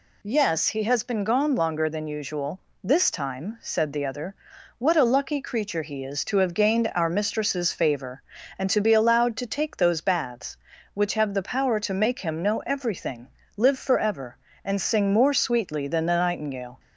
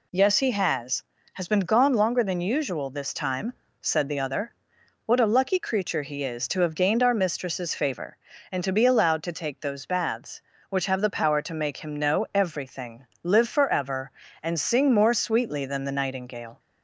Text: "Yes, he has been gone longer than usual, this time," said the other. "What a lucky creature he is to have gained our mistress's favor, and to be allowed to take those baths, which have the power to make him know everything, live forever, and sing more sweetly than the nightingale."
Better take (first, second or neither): first